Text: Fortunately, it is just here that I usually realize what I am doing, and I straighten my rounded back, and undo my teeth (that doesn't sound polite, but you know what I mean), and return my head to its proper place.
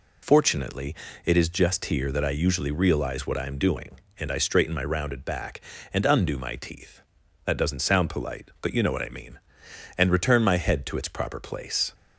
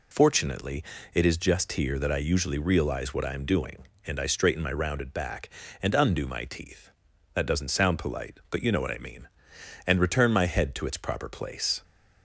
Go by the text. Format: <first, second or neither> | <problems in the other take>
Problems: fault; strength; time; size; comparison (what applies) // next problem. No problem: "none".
neither | none